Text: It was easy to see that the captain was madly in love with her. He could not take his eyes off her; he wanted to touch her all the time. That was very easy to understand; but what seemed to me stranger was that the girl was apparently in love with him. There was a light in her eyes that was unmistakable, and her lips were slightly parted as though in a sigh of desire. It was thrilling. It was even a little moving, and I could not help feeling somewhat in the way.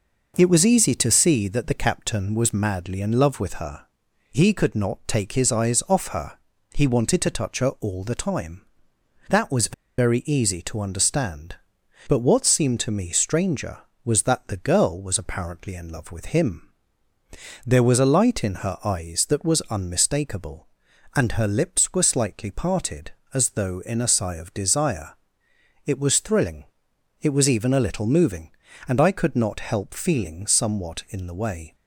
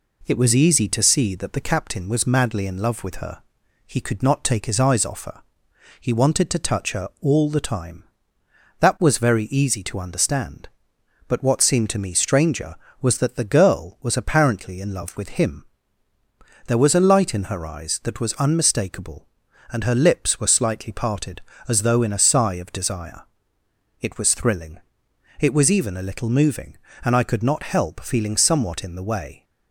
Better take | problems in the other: second | pauses between "was" and "very"; slight; at 9.7 s; 0.26 s long

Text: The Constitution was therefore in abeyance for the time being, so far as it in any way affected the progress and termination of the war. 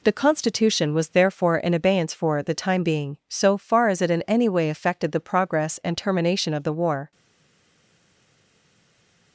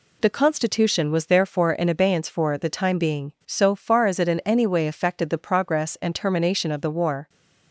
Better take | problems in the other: second | stays silent after the last word; from 7.1 s on; 2.2 s long

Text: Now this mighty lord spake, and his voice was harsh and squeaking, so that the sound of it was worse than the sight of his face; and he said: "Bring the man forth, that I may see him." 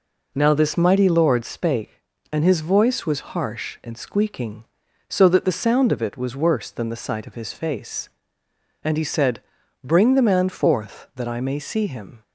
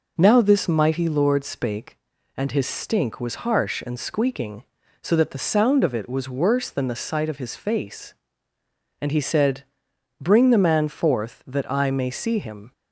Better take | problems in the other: first | says "stink" for "voice"; at 2.6 s

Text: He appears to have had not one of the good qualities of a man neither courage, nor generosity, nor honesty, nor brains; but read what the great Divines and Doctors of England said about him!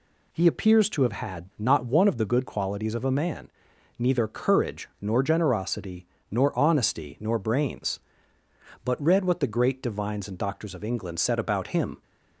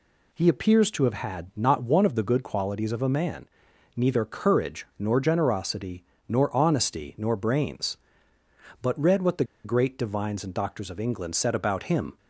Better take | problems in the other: first | pauses between "man" and "neither"; noticeable; at 3.4 s; 0.48 s long; noticeable in the first // pauses between "the" and "great"; slight; at 9.4 s; 0.19 s long

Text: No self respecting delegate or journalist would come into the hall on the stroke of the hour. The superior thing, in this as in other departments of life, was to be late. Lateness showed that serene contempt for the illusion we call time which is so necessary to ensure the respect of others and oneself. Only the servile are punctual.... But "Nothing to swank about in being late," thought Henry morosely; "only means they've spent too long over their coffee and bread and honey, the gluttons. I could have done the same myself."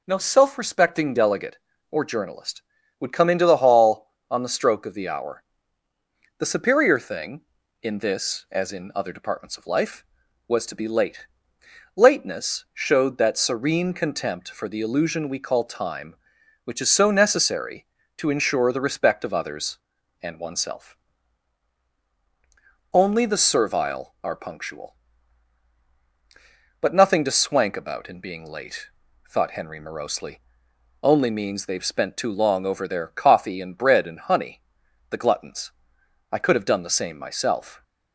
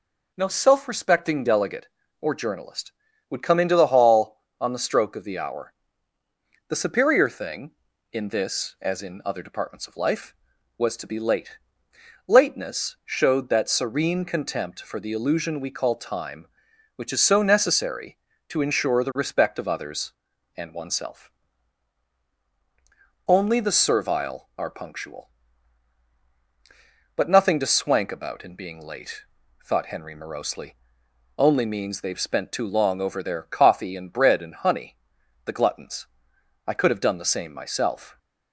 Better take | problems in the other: neither | none

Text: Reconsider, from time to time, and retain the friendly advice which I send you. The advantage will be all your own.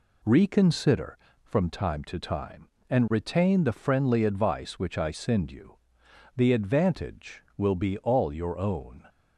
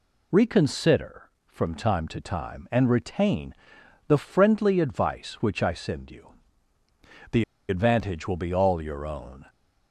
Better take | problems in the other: first | pauses between "retain" and "the"; noticeable; at 3.5 s; 0.54 s long // pauses between "The" and "advantage"; slight; at 7.4 s; 0.24 s long

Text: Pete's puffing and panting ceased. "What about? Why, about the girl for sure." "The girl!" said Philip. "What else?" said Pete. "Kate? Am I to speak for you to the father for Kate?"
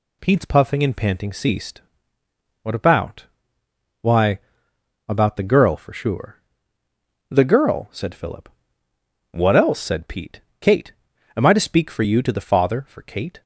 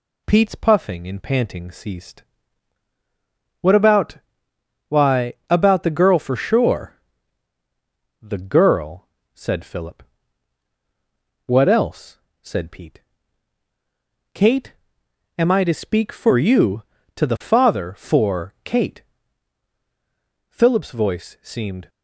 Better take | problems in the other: first | goes on to say "Philip's voice seemed"; from 20.4 s on; 1.4 s long

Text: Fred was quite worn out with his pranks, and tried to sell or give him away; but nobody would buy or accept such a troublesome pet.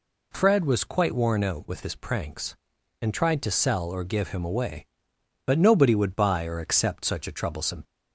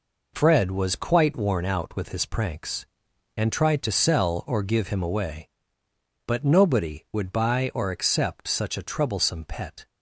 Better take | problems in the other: second | stops before "pet"; at 7.8 s

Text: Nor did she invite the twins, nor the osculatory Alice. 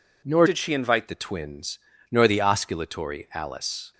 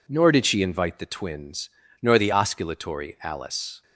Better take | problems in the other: second | changes voice from "did" to "invite"; from 0.4 to 1.0 s; 0.6 s long

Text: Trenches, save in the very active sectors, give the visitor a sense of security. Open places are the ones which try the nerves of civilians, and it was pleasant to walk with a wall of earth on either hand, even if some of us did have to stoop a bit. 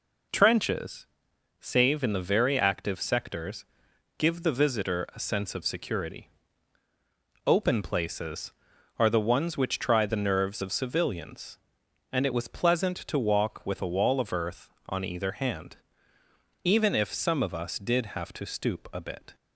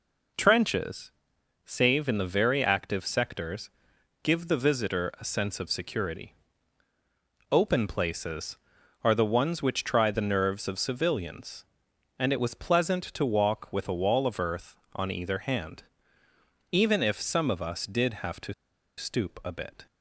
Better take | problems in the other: first | pauses between "to" and "stoop"; at 18.5 s; 0.45 s long

